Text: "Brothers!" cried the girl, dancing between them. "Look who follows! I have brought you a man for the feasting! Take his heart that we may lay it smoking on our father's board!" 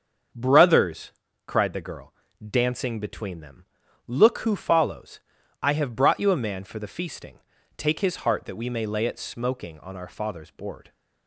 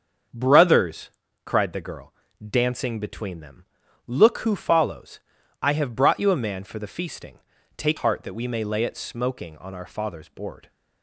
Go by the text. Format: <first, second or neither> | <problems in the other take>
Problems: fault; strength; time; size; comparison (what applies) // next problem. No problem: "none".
first | starts louder than the rest; until 1.6 s; 7 dB; also in the first // skips "his"; at 7.9 s